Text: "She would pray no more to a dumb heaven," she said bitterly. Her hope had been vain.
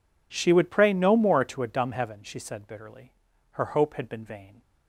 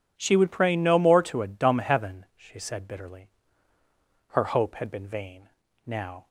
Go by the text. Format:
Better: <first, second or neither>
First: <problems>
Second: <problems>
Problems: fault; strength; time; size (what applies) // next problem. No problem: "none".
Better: first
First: none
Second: goes on to say "Now"; slight; from 5.8 s on; 0.42 s long